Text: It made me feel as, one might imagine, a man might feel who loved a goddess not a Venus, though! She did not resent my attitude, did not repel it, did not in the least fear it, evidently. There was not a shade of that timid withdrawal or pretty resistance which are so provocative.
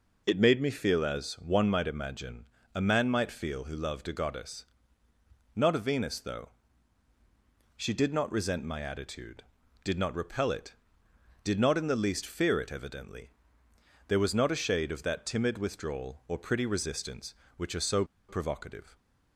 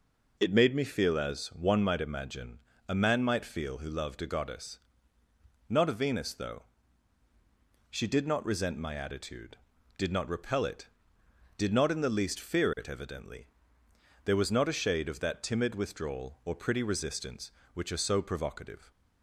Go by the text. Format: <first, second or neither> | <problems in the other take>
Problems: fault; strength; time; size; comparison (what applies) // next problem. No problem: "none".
second | pauses between "goddess" and "not"; noticeable; at 4.6 s; 0.90 s long; noticeable in the second // pauses between "so" and "provocative"; slight; at 18.0 s; 0.25 s long